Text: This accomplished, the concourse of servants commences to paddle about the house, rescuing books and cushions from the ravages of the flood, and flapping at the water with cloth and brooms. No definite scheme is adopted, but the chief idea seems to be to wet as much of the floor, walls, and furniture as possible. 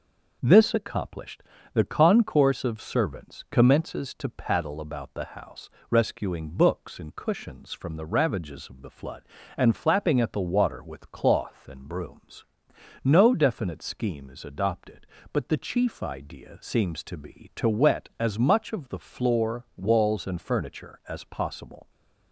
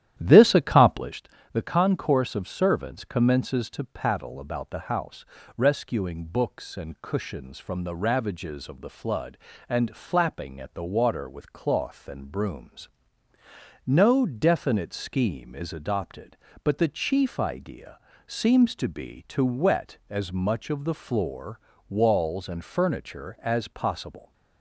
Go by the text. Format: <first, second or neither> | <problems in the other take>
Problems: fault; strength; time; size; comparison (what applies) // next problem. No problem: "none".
first | starts louder than the rest; strong; until 1.2 s; 11.5 dB // pauses between "idea" and "seems"; slight; at 17.9 s; 0.28 s long